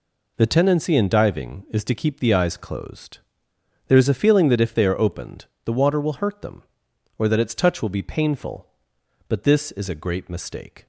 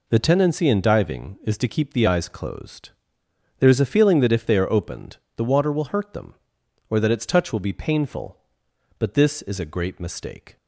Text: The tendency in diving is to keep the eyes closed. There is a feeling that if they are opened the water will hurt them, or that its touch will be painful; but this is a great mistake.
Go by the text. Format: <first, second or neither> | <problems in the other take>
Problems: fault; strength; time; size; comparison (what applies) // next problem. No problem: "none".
neither | pauses between "opened" and "the"; slight; the same in both